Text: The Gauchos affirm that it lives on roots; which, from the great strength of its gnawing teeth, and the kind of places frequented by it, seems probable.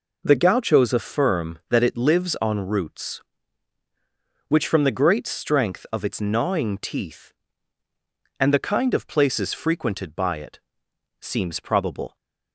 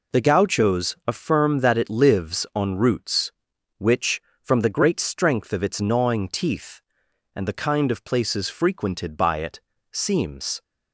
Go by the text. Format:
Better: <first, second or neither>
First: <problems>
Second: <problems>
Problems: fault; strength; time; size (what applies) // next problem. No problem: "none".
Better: first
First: none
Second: stops before "probable"; at 10.6 s